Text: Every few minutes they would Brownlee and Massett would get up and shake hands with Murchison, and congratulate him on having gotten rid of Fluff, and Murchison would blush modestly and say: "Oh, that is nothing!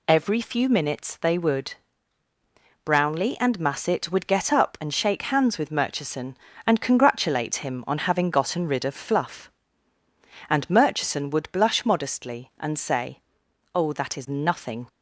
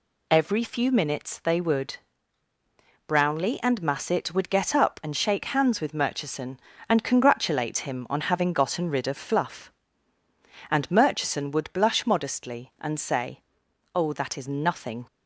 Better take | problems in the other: neither | pauses between "would" and "Brownlee"; the same in both

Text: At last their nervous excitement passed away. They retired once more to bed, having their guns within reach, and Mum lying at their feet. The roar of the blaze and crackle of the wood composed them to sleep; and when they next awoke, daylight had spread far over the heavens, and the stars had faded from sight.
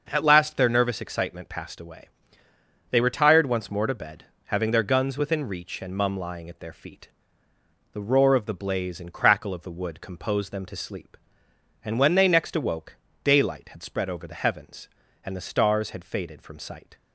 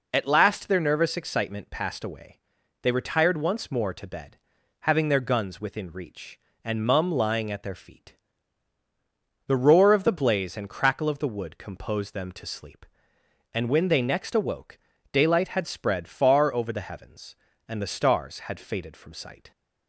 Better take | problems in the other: second | starts louder than the rest; noticeable; until 1.1 s; 6 dB // skips "far"; at 14.0 s

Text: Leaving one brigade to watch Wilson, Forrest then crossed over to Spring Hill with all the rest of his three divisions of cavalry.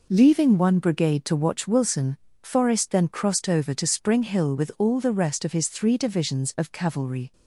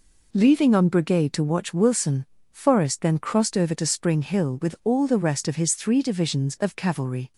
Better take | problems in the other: first | says "on" for "one"; at 0.7 s

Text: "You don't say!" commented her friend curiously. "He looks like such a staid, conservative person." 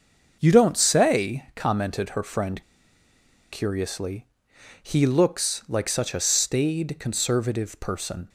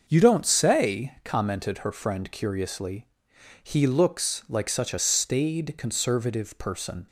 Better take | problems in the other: second | starts louder than the rest; until 1.4 s; 6 dB; also in the second // pauses between "friend" and "curiously"; noticeable; at 2.6 s; 0.89 s long

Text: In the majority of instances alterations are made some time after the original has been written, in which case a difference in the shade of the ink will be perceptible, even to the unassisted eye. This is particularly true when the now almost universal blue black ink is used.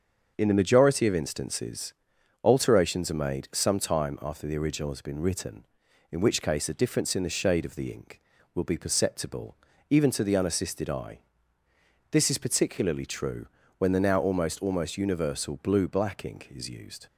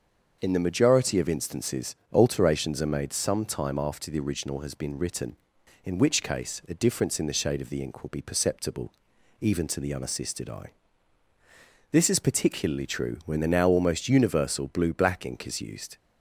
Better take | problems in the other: second | starts louder than the rest; until 1.3 s; 6.5 dB; also in the second // pauses between "instances" and "alterations"; noticeable; at 1.9 s; 0.48 s long; slight in the second // pauses between "true" and "when"; slight; at 13.4 s; 0.32 s long // says "almost" twice; at 14.6 s

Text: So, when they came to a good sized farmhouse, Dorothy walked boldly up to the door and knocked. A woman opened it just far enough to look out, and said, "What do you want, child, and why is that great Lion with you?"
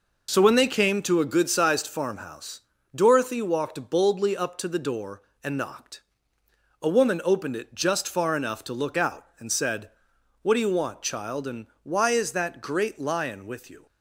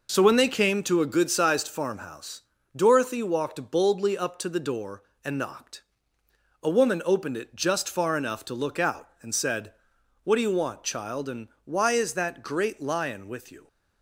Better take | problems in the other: neither | pauses between "and" and "why"; slight; the same in both

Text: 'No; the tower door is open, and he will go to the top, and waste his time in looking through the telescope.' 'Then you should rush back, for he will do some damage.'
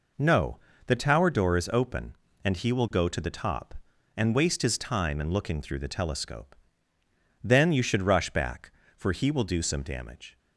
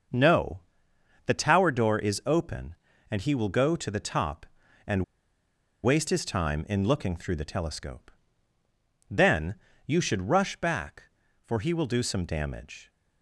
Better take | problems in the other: first | starts louder than the rest; noticeable; until 1.7 s; 6 dB // pauses between "and" and "waste"; noticeable; at 5.0 s; 0.79 s long // pauses between "Then" and "you"; slight; at 9.5 s; 0.30 s long

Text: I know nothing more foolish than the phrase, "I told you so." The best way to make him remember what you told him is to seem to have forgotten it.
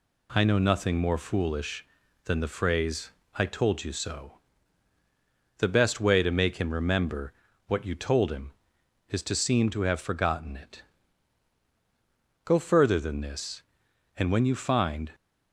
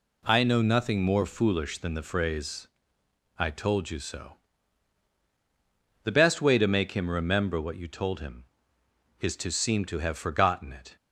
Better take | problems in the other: second | pauses between "remember" and "what"; slight; at 7.3 s; 0.34 s long // goes on to say "Go further than this and when you find"; strong; from 12.4 s on; 2.6 s long

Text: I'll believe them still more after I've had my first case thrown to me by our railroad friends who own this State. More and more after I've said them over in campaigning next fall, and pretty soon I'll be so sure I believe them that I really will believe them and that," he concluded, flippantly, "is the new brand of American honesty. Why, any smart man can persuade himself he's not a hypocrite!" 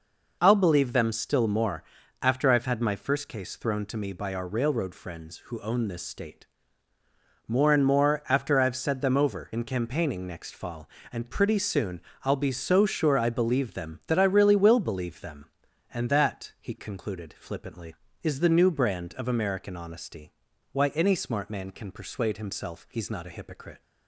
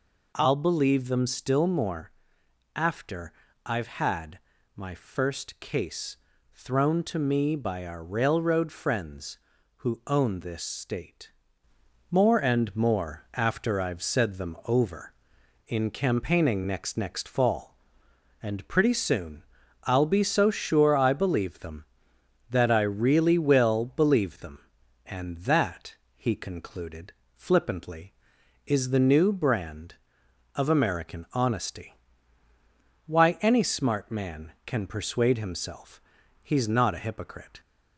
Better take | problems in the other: first | pauses between "more" and "after"; noticeable; at 2.1 s; 0.64 s long; also in the first // pauses between "after" and "I've"; slight; at 3.3 s; 0.33 s long // pauses between "had" and "my"; slight; at 4.3 s; 0.36 s long // pauses between "case" and "thrown"; slight; at 6.1 s; 0.36 s long // says "next" twice; at 16.9 s // pauses between "soon" and "I'll"; at 19.4 s; 0.40 s long; slight in the first // pauses between "himself" and "he's"; at 35.9 s; 0.42 s long

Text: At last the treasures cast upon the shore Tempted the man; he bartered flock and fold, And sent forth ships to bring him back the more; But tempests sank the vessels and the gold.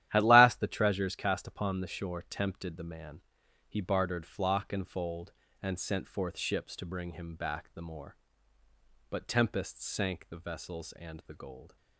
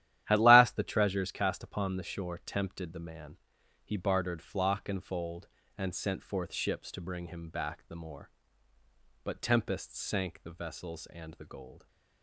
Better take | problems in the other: neither | starts louder than the rest; strong; the same in both

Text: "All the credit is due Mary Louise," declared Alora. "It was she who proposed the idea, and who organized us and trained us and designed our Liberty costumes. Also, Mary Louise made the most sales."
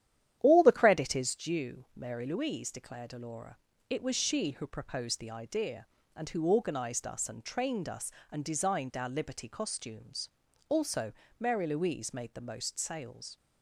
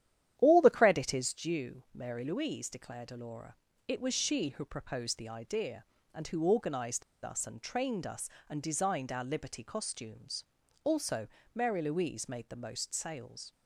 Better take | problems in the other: first | starts louder than the rest; strong; until 1.3 s; 11 dB; strong in the first // pauses between "organized" and "us"; slight; at 7.0 s; 0.22 s long

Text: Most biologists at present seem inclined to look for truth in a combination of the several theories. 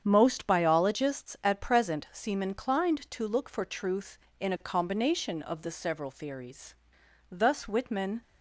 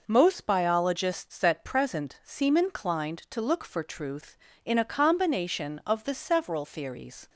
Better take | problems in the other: second | starts louder than the rest; strong; until 1.0 s; 8 dB // goes on to say "Thus Whitman"; noticeable; from 7.3 s on; 0.90 s long

